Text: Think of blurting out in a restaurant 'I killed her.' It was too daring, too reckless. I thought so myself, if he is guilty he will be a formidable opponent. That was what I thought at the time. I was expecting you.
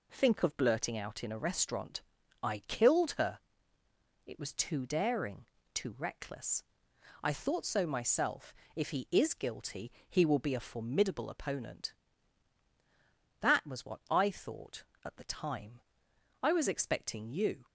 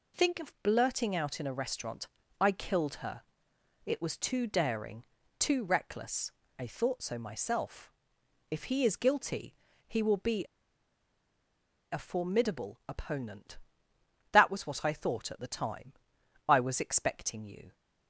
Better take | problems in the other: first | pauses between "restaurant" and "I"; slight; at 2.0 s; 0.34 s long; also in the first // pauses between "guilty" and "he"; slight; at 9.5 s; 0.32 s long; slight in the first // pauses between "be" and "a"; strong; at 10.4 s; 1.4 s long

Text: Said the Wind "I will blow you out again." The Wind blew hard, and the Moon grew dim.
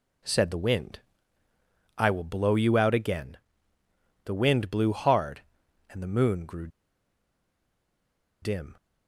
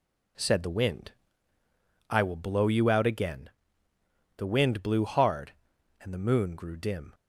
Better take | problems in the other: second | pauses between "Wind" and "I"; noticeable; at 1.0 s; 0.96 s long; noticeable in the second // pauses between "grew" and "dim"; strong; at 6.6 s; 1.7 s long

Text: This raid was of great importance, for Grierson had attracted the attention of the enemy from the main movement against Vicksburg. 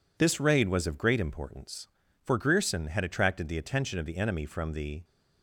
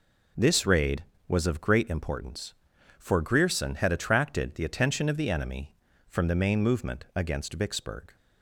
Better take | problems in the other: second | stops before "main movement against Vicksburg"; at 5.0 s

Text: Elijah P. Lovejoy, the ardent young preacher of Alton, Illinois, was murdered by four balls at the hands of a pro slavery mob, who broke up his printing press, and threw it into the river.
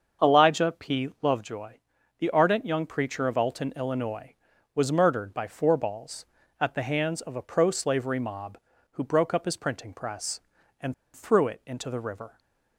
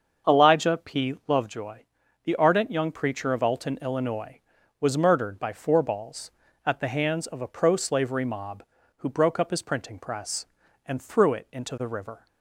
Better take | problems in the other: second | starts louder than the rest; until 1.3 s; 7 dB; also in the second // pauses between "and" and "threw"; slight; at 10.9 s; 0.22 s long

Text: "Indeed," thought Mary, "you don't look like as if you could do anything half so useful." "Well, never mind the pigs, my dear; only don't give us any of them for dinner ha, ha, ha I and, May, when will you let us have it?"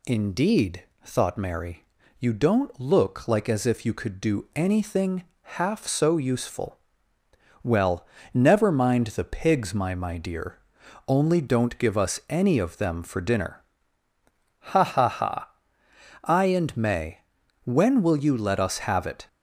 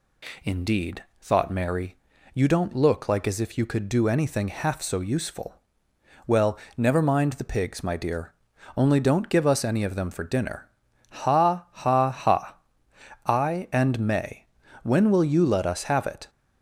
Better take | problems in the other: second | pauses between "anything" and "half"; slight; at 5.2 s; 0.18 s long // says "my" twice; at 9.9 s // pauses between "dinner" and "ha"; at 13.6 s; 1.1 s long; also in the second // pauses between "ha" and "I"; noticeable; at 15.5 s; 0.72 s long; noticeable in the second

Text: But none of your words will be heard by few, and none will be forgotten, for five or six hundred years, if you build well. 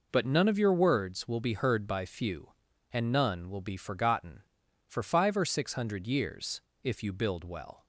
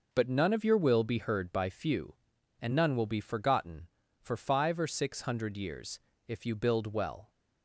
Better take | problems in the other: first | skips "words"; at 0.7 s

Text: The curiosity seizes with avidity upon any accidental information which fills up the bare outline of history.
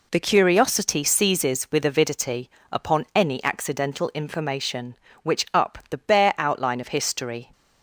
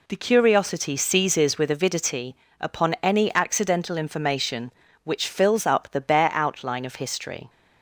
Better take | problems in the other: second | pauses between "avidity" and "upon"; slight; at 2.4 s; 0.22 s long; slight in the second // skips "fills"; at 5.4 s

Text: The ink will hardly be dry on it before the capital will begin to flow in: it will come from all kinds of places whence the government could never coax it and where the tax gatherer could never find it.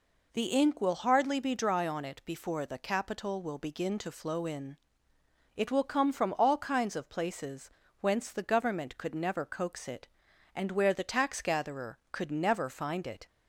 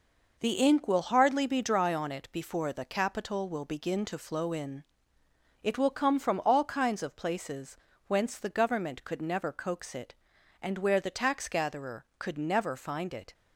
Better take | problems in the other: first | gets quieter; throughout; 6 dB // pauses between "places" and "whence"; slight; at 7.7 s; 0.30 s long; slight in the first

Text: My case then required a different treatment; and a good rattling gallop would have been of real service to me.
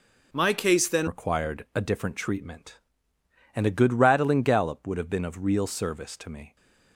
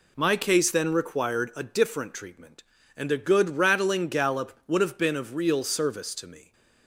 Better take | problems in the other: second | changes voice at "required"; from 1.0 s on; 5.5 s long

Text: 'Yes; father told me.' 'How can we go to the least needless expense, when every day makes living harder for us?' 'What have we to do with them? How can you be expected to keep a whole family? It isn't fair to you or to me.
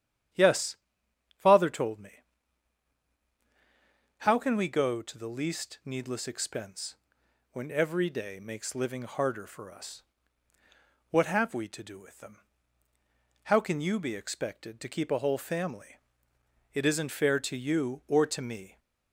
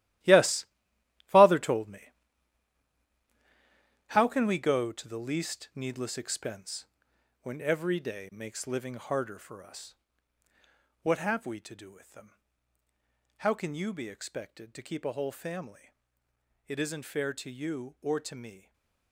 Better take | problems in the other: first | gets quieter; strong; throughout; 11.5 dB // starts louder than the rest; strong; until 1.8 s; 14 dB; strong in the first // stays silent after the last word; slight; from 18.5 s on; 0.6 s long

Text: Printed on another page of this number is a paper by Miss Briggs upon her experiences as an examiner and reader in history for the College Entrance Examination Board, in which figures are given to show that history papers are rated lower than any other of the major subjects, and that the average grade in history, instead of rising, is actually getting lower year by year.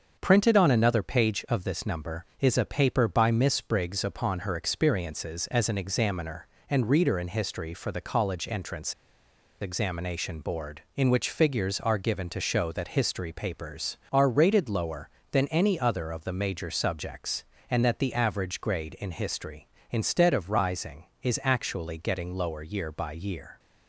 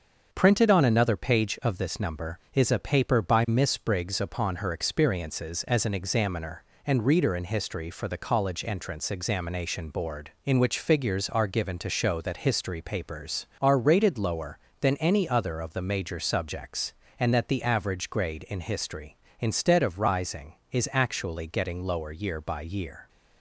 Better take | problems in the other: second | starts louder than the rest; until 1.2 s; 6.5 dB; also in the second // pauses between "Entrance" and "Examination"; noticeable; at 8.9 s; 0.67 s long

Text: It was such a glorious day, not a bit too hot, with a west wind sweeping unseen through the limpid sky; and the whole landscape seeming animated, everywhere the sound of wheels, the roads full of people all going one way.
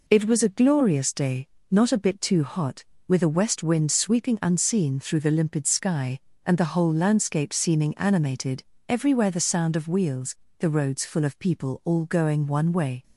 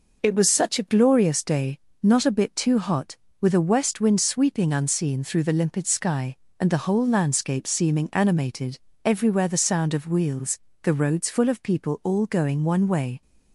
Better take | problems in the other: second | skips "such"; at 0.4 s

